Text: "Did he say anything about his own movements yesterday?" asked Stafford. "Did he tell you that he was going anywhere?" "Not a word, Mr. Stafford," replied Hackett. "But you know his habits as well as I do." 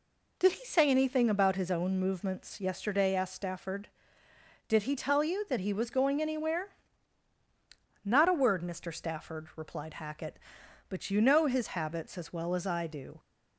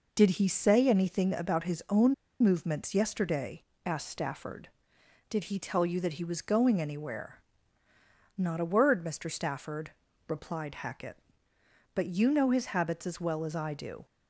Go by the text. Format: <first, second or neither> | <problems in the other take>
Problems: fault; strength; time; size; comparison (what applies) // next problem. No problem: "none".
first | pauses between "own" and "movements"; slight; at 2.1 s; 0.28 s long